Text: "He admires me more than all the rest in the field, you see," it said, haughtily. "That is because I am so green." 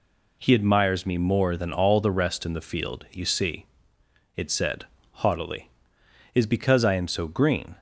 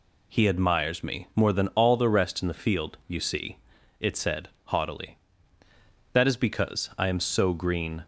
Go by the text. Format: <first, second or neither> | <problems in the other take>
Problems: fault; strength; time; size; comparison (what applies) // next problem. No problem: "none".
second | skips "That"; at 6.0 s